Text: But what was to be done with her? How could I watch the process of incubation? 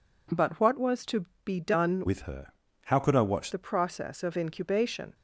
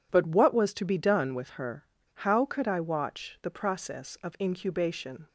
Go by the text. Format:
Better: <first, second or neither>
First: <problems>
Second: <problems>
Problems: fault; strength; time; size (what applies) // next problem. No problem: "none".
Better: second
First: pauses between "to" and "be"; slight; at 1.2 s; 0.18 s long // changes voice from "with" to "watch"; from 2.0 to 3.5 s; 1.5 s long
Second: none